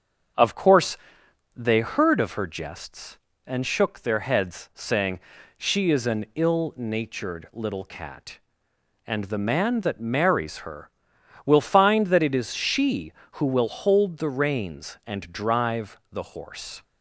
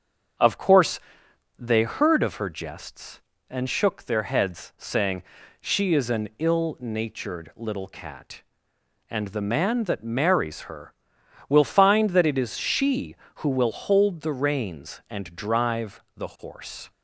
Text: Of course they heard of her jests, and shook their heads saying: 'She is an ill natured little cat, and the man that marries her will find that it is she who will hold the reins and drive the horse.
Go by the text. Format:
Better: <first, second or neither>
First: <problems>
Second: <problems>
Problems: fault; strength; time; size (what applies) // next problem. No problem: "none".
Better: neither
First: starts louder than the rest; until 1.9 s; 7 dB // pauses between "course" and "they"; noticeable; at 0.9 s; 0.58 s long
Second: starts louder than the rest; until 1.9 s; 7 dB // pauses between "course" and "they"; noticeable; at 0.9 s; 0.58 s long